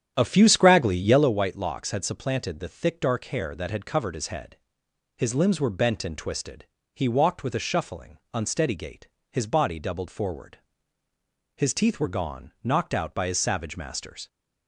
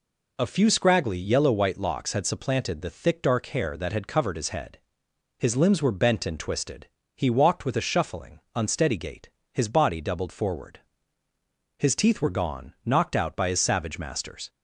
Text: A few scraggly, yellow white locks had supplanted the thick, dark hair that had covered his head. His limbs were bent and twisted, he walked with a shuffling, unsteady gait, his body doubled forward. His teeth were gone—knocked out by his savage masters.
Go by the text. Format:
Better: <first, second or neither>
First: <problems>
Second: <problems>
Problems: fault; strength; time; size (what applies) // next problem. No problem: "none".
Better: second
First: starts louder than the rest; strong; until 1.3 s; 9.5 dB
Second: none